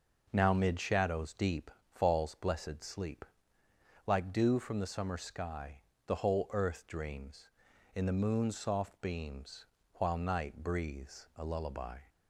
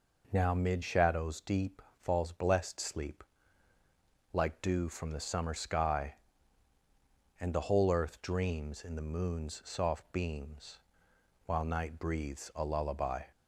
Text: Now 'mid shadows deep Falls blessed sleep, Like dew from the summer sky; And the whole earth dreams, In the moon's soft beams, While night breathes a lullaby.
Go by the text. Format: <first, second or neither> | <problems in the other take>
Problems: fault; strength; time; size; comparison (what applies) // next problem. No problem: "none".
second | pauses between "deep" and "Falls"; slight; at 1.7 s; 0.24 s long; slight in the second // skips "And"; at 5.9 s